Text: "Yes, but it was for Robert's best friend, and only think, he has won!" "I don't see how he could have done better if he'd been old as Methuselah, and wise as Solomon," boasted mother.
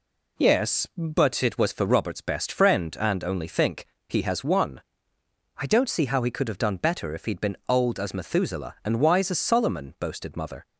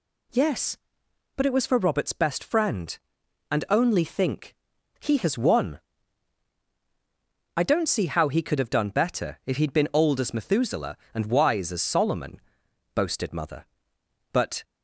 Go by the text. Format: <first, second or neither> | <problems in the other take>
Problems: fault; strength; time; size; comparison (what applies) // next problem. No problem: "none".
first | goes on to say "But"; slight; from 14.3 s on; 0.32 s long